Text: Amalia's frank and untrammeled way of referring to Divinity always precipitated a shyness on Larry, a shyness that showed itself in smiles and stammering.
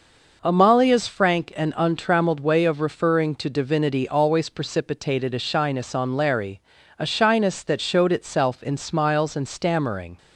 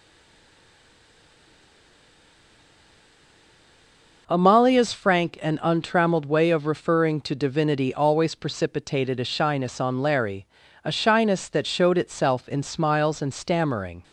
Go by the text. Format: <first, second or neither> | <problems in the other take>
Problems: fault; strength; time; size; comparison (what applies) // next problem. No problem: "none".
first | stays silent before the first word; strong; until 4.2 s; 4.2 s long